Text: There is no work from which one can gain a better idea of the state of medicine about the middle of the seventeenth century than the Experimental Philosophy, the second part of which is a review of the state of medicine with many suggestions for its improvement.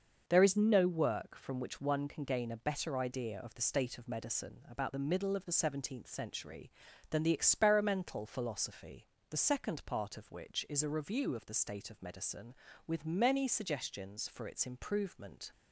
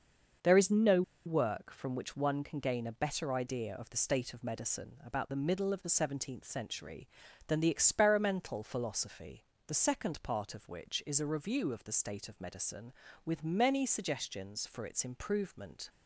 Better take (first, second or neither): first